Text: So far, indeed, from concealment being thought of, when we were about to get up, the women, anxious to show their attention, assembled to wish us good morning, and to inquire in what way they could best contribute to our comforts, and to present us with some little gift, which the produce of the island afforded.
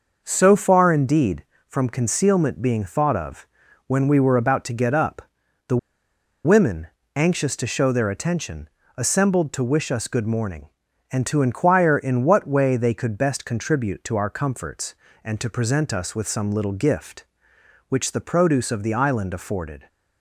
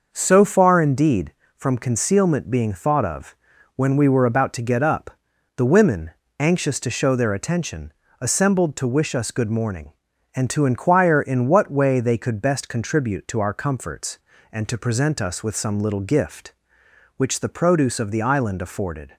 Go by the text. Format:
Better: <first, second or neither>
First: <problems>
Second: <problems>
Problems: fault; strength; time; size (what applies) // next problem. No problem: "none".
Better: second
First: pauses between "the" and "women"; noticeable; at 5.7 s; 0.68 s long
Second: none